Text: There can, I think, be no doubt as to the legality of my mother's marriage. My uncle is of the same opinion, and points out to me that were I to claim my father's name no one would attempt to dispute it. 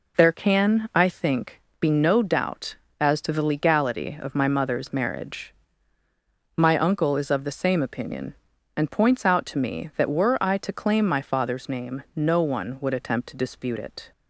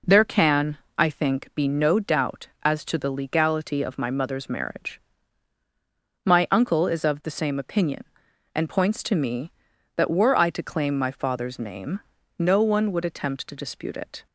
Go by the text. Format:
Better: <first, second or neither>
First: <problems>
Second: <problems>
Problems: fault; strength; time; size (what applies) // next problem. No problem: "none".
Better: first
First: none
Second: skips "out"; at 9.0 s // pauses between "name" and "no"; at 12.0 s; 0.38 s long